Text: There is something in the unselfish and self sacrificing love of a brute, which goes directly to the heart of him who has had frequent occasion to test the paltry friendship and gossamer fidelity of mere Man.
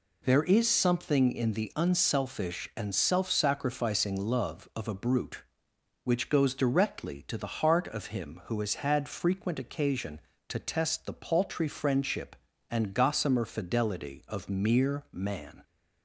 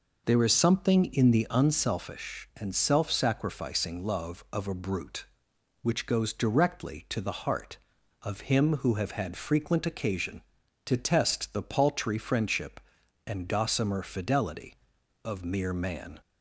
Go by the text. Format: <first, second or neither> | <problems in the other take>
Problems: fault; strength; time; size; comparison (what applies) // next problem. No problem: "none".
first | says "have" for "has"; at 8.9 s